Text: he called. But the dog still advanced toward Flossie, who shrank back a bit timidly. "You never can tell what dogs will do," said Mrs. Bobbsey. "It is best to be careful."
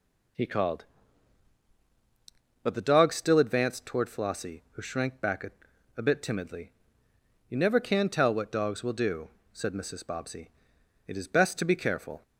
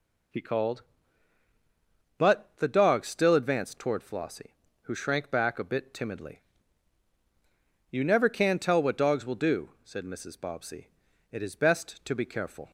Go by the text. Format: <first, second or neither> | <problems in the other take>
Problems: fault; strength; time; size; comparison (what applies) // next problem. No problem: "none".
second | says "a" twice; at 5.9 s